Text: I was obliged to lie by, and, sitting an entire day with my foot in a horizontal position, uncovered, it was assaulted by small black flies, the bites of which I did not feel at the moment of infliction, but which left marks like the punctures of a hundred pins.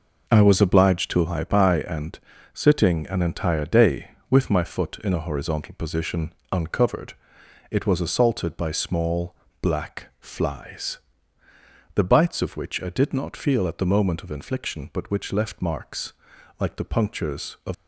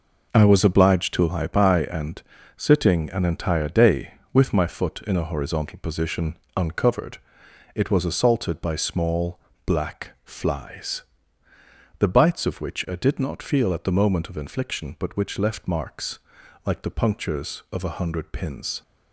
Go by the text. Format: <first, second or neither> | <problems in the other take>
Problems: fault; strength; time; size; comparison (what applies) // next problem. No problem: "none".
second | pauses between "small" and "black"; slight; at 9.3 s; 0.26 s long; slight in the second // pauses between "marks" and "like"; noticeable; at 16.1 s; 0.48 s long; noticeable in the second // stops before "a hundred pins"; at 17.7 s